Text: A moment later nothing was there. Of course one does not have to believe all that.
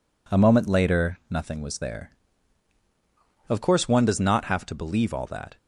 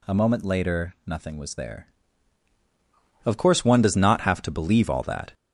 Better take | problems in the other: first | gets louder; noticeable; throughout; 5 dB

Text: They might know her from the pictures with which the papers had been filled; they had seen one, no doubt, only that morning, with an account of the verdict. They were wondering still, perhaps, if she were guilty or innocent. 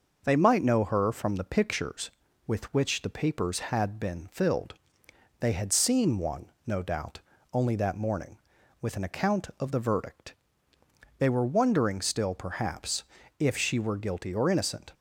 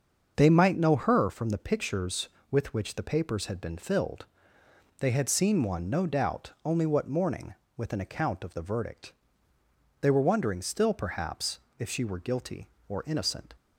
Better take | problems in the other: first | starts louder than the rest; until 1.3 s; 6.5 dB // says "what" for "that"; at 6.8 s

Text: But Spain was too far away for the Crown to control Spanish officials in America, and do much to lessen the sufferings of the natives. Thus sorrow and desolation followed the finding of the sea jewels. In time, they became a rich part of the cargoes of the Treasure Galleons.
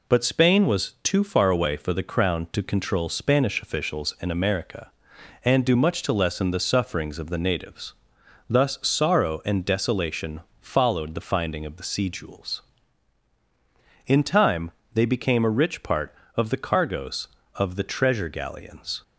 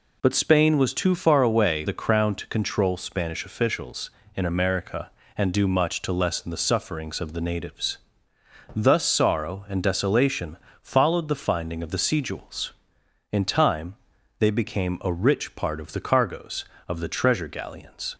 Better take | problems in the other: first | skips "for"; at 1.8 s // pauses between "desolation" and "followed"; slight; at 10.5 s; 0.24 s long; slight in the first

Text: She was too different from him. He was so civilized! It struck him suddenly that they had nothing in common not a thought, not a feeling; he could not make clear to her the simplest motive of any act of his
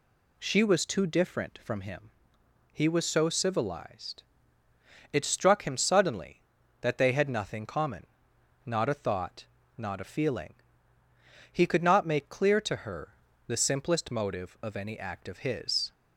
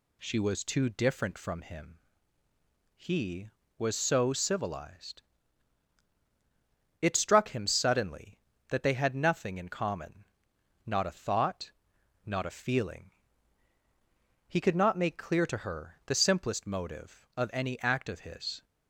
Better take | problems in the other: second | skips "in"; at 7.6 s // pauses between "common" and "not"; noticeable; at 8.0 s; 0.60 s long; noticeable in the second // pauses between "her" and "the"; slight; at 13.1 s; 0.34 s long

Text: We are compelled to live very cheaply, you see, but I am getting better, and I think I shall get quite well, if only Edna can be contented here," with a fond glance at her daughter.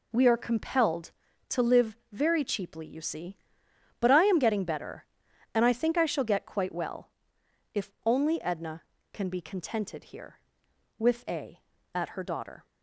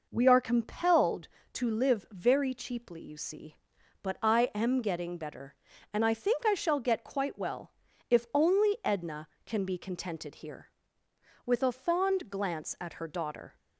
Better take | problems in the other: second | pauses between "live" and "very"; slight; at 1.9 s; 0.16 s long // skips "fond glance"; at 11.7 s

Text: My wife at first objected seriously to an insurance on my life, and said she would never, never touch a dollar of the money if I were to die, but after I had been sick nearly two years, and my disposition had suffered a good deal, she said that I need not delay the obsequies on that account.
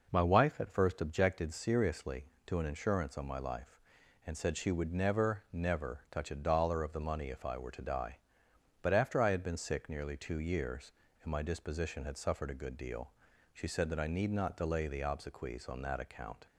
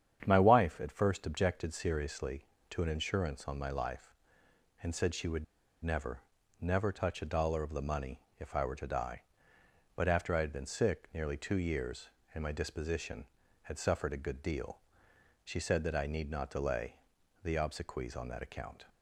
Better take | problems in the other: first | starts louder than the rest; strong; until 1.2 s; 8.5 dB // pauses between "would" and "never"; at 5.4 s; 0.39 s long // pauses between "money" and "if"; slight; at 8.1 s; 0.20 s long // pauses between "delay" and "the"; noticeable; at 16.9 s; 0.50 s long

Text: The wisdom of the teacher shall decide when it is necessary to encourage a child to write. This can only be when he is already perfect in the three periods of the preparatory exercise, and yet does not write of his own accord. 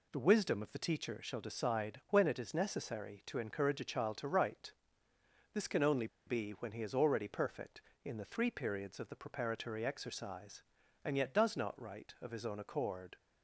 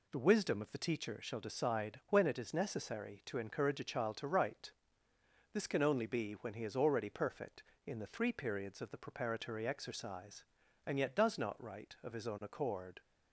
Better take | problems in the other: second | pauses between "only" and "be"; slight; at 6.0 s; 0.20 s long

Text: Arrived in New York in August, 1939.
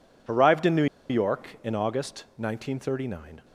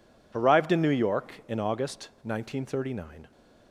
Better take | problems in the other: second | pauses between "New" and "York"; slight; at 0.8 s; 0.24 s long

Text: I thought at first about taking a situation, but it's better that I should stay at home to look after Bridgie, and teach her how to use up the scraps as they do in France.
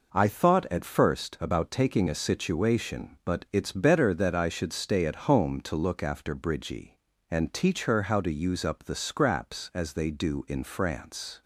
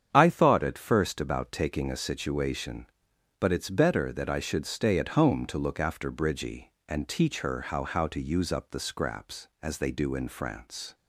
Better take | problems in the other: first | starts louder than the rest; strong; until 1.1 s; 8.5 dB // says "how" twice; at 7.8 s

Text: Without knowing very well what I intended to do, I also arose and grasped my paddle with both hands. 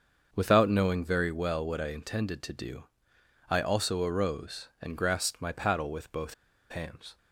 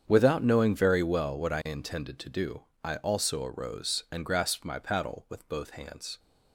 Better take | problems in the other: second | starts louder than the rest; until 1.3 s; 6.5 dB; strong in the second // pauses between "both" and "hands"; at 6.3 s; 0.36 s long

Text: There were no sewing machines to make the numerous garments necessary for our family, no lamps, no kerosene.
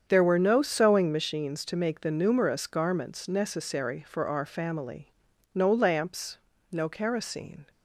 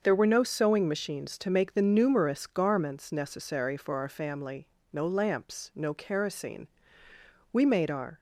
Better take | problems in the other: first | starts louder than the rest; until 1.0 s; 6.5 dB; strong in the first // goes on to say "We made our"; noticeable; from 7.5 s on; 0.66 s long

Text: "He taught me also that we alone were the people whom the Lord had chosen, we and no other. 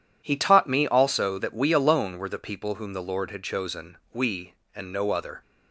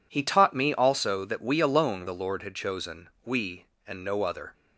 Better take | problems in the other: first | skips "were the people whom"; at 2.0 s

